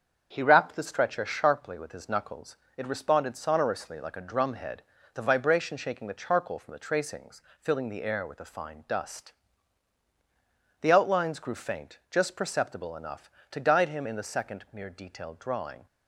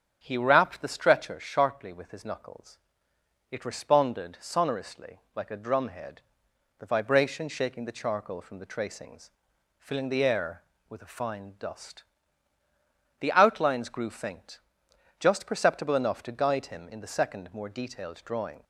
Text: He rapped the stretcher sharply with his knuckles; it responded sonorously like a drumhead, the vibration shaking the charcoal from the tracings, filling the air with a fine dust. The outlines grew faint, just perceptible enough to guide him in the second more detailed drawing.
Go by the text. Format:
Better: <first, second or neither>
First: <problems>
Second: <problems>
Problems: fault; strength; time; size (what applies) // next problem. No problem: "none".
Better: second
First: starts louder than the rest; strong; until 1.3 s; 7 dB // says "mere" for "more"; at 14.7 s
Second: starts louder than the rest; strong; until 1.2 s; 8.5 dB